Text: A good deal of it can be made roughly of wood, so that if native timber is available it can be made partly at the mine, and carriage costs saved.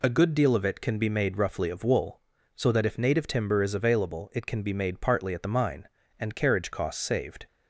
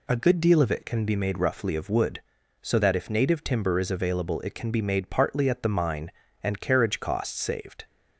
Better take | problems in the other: second | says "wool" for "wood"; at 1.8 s

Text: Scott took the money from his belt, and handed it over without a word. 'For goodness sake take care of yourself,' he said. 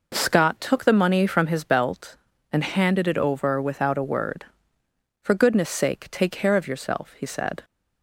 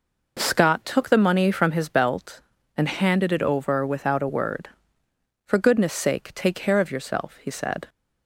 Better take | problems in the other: neither | none

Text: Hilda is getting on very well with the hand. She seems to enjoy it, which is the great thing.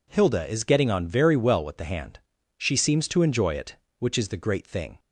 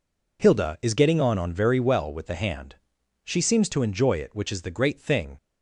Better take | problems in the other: first | says "on" twice; at 1.3 s

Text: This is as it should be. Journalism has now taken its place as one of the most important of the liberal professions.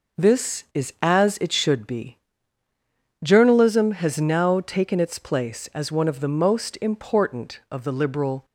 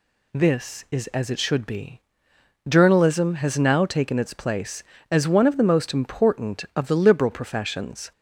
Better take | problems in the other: second | stops before "professions"; at 8.4 s

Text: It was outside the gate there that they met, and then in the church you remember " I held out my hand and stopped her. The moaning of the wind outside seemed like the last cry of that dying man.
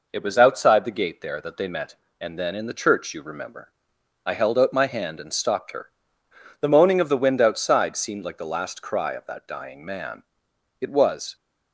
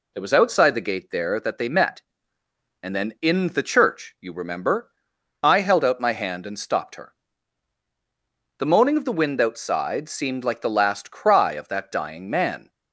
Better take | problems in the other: second | goes on to say "It was"; from 10.8 s on; 0.54 s long

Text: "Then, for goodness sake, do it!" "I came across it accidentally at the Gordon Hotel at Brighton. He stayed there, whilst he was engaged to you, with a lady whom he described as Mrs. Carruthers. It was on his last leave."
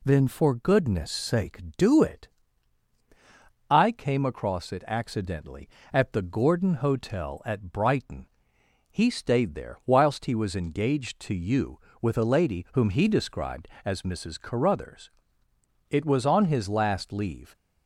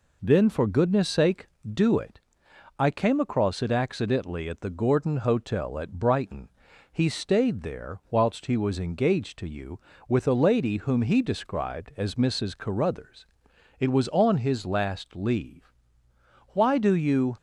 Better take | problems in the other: first | goes on to say "Why do you"; noticeable; from 16.5 s on; 0.82 s long

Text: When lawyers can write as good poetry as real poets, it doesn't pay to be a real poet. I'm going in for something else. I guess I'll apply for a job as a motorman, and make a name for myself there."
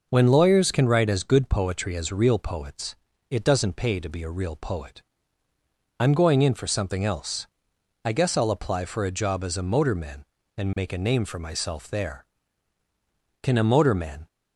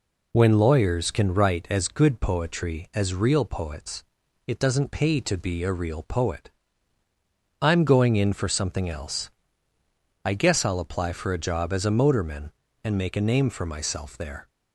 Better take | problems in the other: second | goes on to say "Can a motorman"; noticeable; from 13.4 s on; 0.86 s long

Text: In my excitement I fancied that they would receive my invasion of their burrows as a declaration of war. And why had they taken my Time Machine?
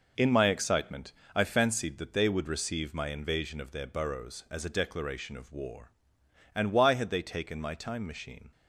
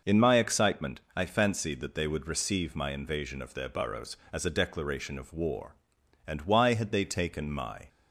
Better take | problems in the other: first | pauses between "excitement" and "I"; slight; at 0.9 s; 0.16 s long; slight in the first // stops before "Time Machine"; at 7.8 s

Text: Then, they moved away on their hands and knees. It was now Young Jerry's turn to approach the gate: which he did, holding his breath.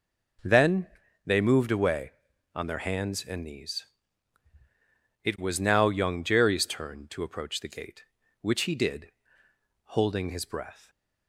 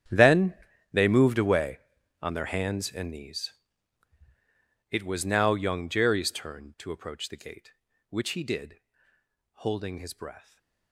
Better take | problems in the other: first | gets quieter; strong; throughout; 19 dB // stays silent after the last word; slight; from 10.3 s on; 0.6 s long; slight in the first

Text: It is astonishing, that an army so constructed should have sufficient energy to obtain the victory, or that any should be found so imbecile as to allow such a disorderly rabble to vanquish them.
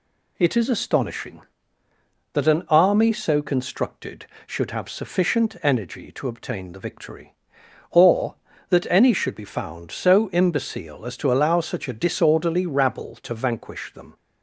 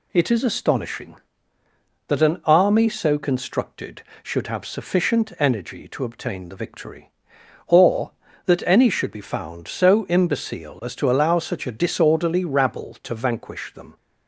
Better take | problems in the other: neither | none

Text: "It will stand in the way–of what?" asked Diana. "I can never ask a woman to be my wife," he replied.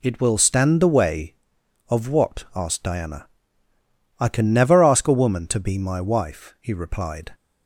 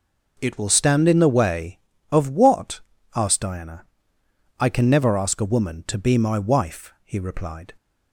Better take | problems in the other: second | skips "in"; at 0.8 s

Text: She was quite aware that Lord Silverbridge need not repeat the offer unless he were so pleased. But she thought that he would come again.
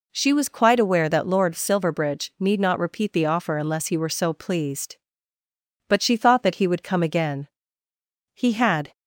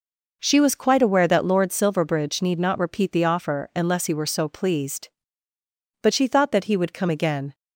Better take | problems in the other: second | goes on to say "He had"; from 8.3 s on; 0.58 s long

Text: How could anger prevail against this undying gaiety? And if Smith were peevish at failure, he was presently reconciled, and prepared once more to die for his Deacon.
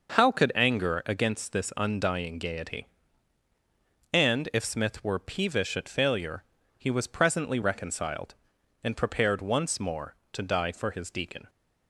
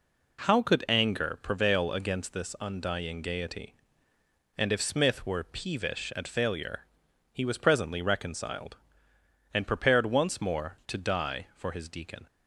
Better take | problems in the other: second | skips "prevail"; at 1.0 s

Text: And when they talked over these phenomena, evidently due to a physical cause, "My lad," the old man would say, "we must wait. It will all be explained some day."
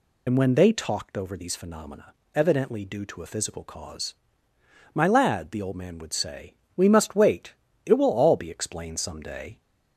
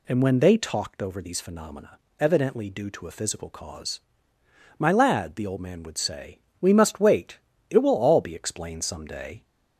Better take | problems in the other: second | loses the start of "And"; at 0.2 s; 45 ms

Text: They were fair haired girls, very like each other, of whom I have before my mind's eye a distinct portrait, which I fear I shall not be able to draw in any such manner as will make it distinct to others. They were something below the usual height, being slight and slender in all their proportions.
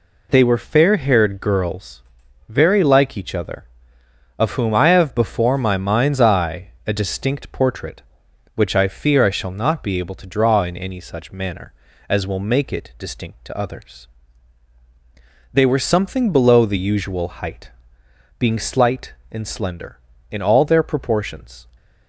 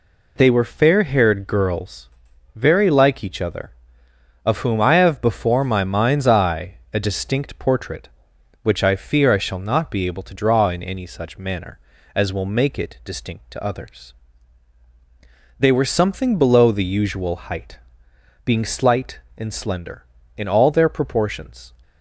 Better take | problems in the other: neither | pauses between "eye" and "a"; slight; the same in both

